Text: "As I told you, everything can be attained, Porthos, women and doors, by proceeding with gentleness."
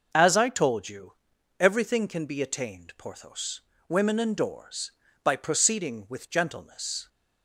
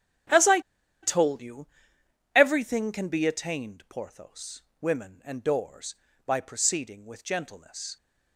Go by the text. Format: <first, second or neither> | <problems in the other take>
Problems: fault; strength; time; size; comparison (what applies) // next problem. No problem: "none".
first | starts louder than the rest; strong; until 2.4 s; 10.5 dB // pauses between "I" and "told"; at 0.6 s; 0.42 s long